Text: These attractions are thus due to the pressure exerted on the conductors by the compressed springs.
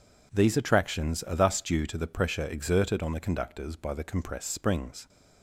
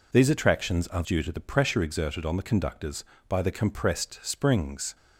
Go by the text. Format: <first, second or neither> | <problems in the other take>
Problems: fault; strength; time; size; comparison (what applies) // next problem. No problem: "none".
first | skips "thus"; at 1.0 s